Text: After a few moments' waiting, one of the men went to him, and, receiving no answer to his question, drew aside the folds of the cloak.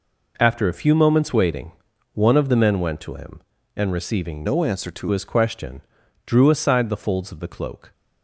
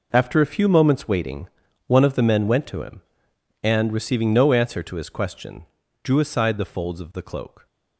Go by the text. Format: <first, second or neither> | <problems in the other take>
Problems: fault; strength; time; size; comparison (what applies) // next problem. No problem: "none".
second | changes voice from "no" to "to"; from 4.4 to 5.0 s; 0.6 s long